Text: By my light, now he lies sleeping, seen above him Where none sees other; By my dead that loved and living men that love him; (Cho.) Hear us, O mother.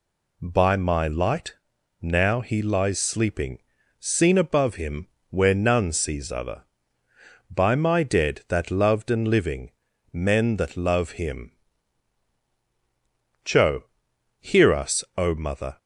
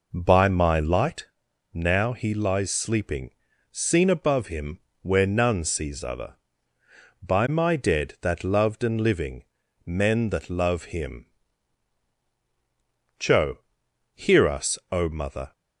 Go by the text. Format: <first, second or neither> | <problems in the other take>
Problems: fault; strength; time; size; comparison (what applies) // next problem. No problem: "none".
first | starts louder than the rest; noticeable; until 1.2 s; 5 dB // pauses between "him" and "Where"; slight; at 4.7 s; 0.24 s long; slight in the first // pauses between "living" and "men"; at 9.4 s; 0.42 s long; also in the first